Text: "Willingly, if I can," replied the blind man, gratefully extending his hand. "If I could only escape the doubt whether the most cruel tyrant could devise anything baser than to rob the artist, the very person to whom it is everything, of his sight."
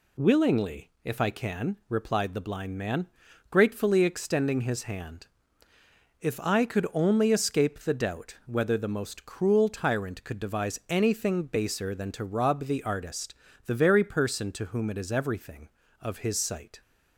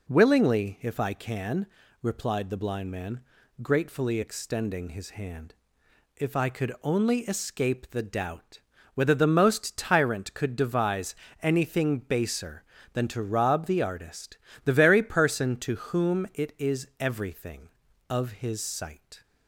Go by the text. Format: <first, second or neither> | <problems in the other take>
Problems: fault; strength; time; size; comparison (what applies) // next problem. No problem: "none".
first | pauses between "doubt" and "whether"; slight; at 8.5 s; 0.34 s long // skips "cruel"; at 9.7 s // pauses between "devise" and "anything"; slight; at 11.1 s; 0.26 s long